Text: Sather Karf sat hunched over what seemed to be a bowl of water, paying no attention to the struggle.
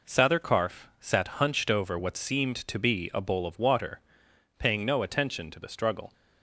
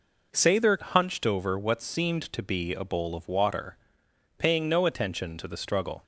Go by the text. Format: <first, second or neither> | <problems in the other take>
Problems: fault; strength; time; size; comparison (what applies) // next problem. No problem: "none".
first | skips "Karf sat"; at 0.8 s